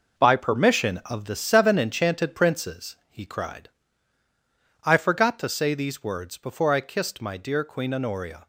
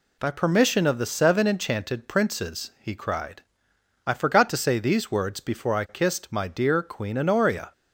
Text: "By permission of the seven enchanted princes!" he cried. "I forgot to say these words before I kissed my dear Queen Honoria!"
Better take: second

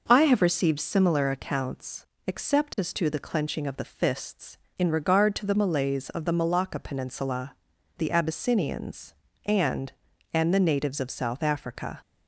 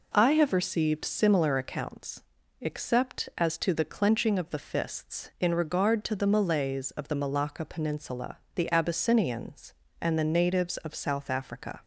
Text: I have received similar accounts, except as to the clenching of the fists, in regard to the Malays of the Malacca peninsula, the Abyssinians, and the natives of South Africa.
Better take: second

